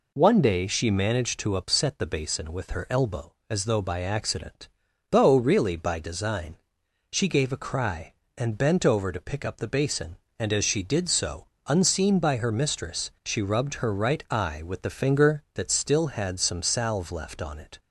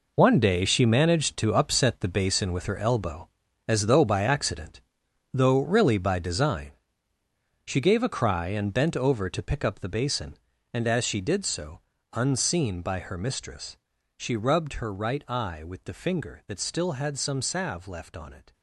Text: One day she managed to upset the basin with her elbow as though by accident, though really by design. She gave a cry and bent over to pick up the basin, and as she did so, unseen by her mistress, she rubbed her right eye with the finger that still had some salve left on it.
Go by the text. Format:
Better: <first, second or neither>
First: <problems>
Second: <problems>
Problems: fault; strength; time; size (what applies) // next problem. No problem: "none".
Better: first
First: none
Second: gets quieter; strong; throughout; 10.5 dB